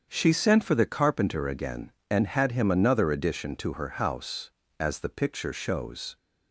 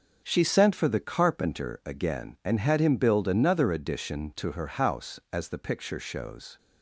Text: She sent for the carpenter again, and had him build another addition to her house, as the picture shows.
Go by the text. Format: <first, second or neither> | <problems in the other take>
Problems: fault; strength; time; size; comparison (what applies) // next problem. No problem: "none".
second | starts louder than the rest; strong; until 1.1 s; 7.5 dB; also in the second // skips "build"; at 2.7 s